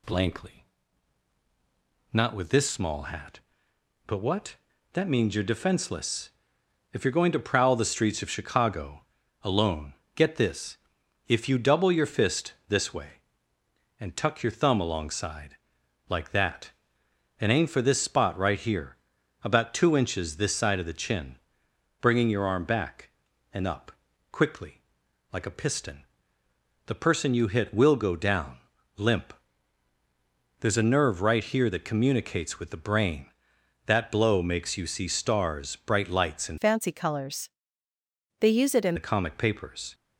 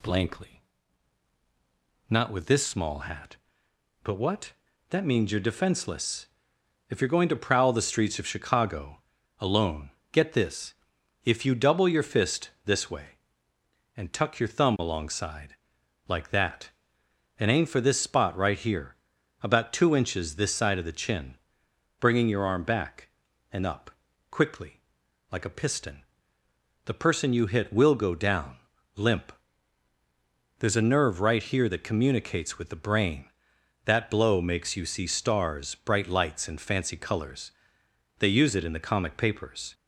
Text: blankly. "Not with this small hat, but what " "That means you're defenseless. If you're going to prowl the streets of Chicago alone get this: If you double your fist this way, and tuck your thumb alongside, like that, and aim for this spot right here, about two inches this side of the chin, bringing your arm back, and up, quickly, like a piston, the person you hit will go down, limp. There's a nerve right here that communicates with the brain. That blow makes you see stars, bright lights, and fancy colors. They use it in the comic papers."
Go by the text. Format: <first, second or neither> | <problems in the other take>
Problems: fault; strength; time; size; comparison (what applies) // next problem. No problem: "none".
second | pauses between "Chicago" and "alone"; at 9.0 s; 0.38 s long; also in the second // pauses between "alone" and "get"; slight; at 9.9 s; 0.20 s long; slight in the second // pauses between "fist" and "this"; slight; at 12.5 s; 0.16 s long; slight in the second // changes voice from "fancy" to "in"; from 36.5 to 38.9 s; 2.4 s long